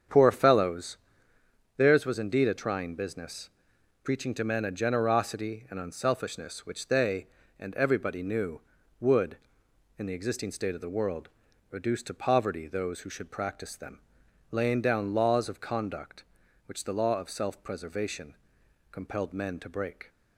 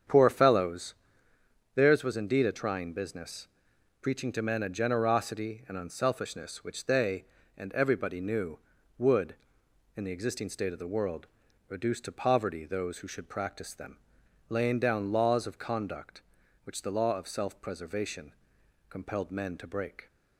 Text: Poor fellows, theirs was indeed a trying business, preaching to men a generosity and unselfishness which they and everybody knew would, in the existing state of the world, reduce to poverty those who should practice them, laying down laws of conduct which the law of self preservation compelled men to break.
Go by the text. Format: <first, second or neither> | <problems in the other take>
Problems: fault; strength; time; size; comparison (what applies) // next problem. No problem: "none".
neither | starts louder than the rest; strong; the same in both // pauses between "preservation" and "compelled"; noticeable; the same in both